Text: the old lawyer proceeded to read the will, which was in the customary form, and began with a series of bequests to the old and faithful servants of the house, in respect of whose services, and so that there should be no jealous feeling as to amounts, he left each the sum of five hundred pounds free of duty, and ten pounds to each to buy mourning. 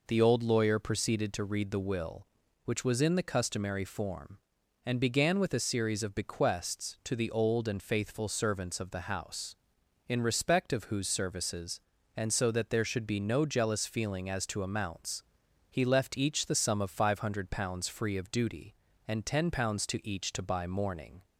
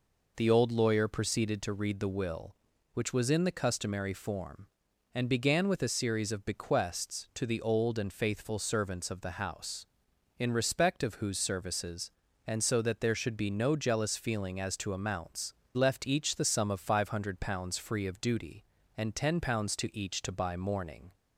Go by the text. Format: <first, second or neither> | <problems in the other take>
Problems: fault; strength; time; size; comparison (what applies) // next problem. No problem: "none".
first | skips "he"; at 15.6 s